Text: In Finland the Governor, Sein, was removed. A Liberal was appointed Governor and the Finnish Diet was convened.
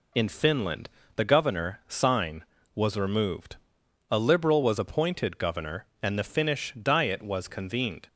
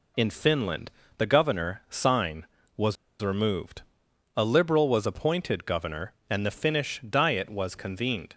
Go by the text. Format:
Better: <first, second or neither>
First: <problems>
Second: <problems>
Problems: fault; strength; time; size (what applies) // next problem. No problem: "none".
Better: first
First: pauses between "Finland" and "the"; slight; at 0.8 s; 0.28 s long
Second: pauses between "Finland" and "the"; slight; at 0.9 s; 0.28 s long // pauses between "was" and "removed"; slight; at 2.9 s; 0.26 s long